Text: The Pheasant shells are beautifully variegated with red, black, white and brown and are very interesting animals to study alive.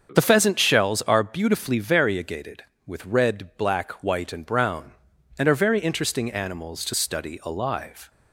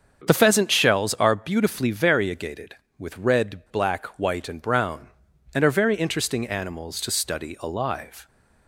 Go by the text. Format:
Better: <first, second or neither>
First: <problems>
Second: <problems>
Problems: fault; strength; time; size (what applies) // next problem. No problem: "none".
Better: neither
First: starts louder than the rest; until 1.1 s; 7 dB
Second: starts louder than the rest; until 1.2 s; 7 dB